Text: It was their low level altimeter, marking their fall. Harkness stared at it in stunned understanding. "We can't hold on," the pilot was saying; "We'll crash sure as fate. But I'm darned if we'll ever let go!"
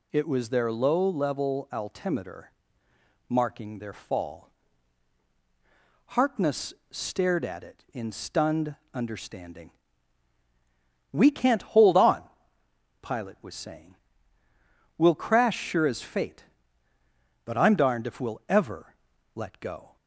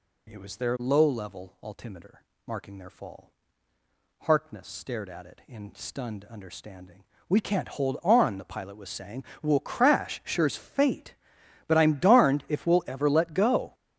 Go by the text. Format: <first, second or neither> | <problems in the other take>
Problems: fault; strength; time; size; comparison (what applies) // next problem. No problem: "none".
second | pauses between "Harkness" and "stared"; slight; at 6.7 s; 0.16 s long // pauses between "stunned" and "understanding"; slight; at 8.7 s; 0.16 s long // skips "the"; at 12.6 s // pauses between "ever" and "let"; at 18.9 s; 0.40 s long